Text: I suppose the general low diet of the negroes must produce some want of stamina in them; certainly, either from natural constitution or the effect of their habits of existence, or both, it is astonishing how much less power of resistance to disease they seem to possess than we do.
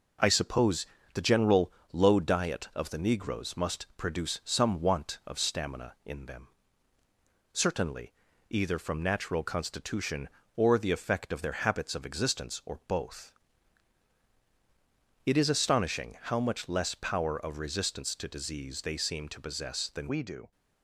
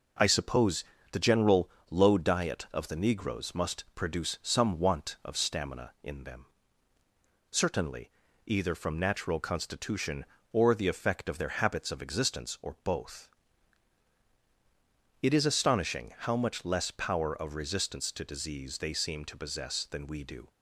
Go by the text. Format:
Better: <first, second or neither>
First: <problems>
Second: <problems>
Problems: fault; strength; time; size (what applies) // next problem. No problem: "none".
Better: second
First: pauses between "suppose" and "the"; slight; at 0.8 s; 0.28 s long // pauses between "general" and "low"; slight; at 1.7 s; 0.20 s long // changes voice at "we"; from 20.0 s on; 0.5 s long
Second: pauses between "suppose" and "the"; slight; at 0.8 s; 0.28 s long // pauses between "general" and "low"; slight; at 1.6 s; 0.20 s long